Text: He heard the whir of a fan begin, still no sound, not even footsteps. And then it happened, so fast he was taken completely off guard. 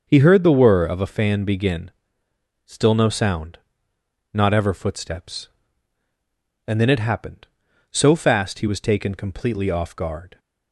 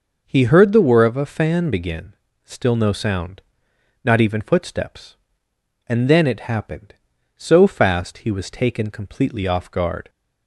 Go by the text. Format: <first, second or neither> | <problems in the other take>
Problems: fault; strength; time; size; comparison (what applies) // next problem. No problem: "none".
second | starts louder than the rest; until 1.0 s; 6.5 dB // says "ever" for "even"; at 4.5 s